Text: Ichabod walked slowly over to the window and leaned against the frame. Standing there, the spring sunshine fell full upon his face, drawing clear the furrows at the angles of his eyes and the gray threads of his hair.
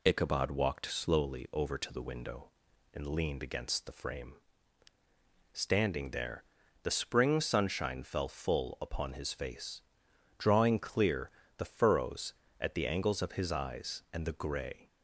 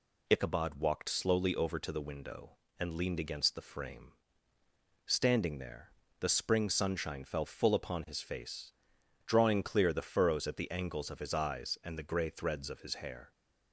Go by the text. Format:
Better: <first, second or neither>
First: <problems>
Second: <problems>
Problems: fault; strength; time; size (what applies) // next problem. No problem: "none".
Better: second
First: pauses between "clear" and "the"; slight; at 11.2 s; 0.30 s long // stops before "threads of his hair"; at 14.8 s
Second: none